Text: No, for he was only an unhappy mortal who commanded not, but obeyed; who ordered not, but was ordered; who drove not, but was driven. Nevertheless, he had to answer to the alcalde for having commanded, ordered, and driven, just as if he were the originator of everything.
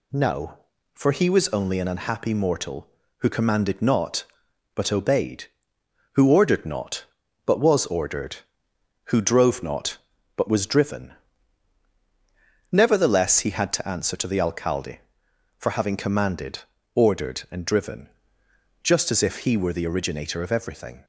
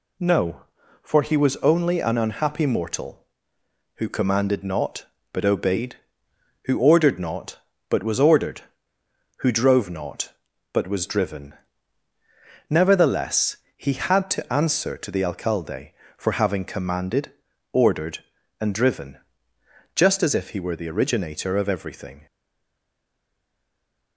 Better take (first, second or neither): first